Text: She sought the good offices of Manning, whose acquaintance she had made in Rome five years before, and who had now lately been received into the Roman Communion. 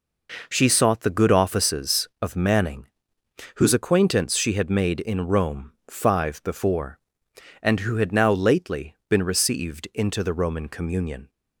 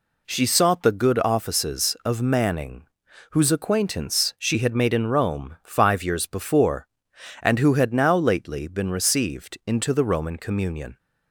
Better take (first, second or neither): second